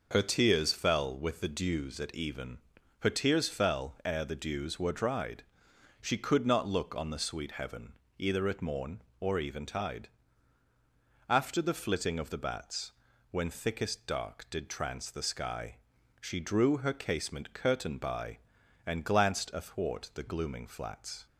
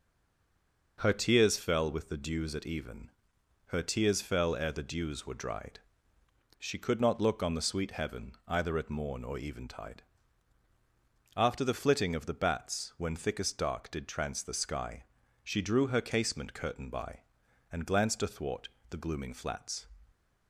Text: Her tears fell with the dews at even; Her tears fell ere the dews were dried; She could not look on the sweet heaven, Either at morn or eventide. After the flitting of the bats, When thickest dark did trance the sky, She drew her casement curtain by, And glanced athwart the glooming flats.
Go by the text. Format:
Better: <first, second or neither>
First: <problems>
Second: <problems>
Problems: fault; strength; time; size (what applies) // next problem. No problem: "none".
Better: first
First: none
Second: stays silent before the first word; slight; until 0.9 s; 0.9 s long // pauses between "athwart" and "the"; slight; at 18.6 s; 0.22 s long